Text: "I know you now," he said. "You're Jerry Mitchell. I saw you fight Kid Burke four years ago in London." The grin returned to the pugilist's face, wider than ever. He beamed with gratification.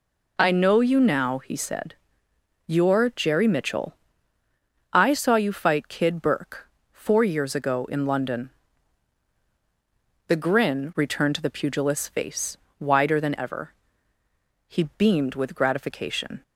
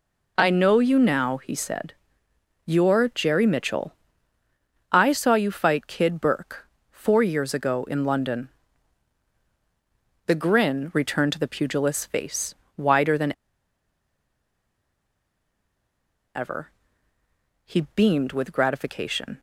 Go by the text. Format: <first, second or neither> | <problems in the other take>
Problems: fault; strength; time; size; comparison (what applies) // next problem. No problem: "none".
first | pauses between "Burke" and "four"; slight; at 6.6 s; 0.22 s long; slight in the first // pauses between "than" and "ever"; strong; at 13.3 s; 3.0 s long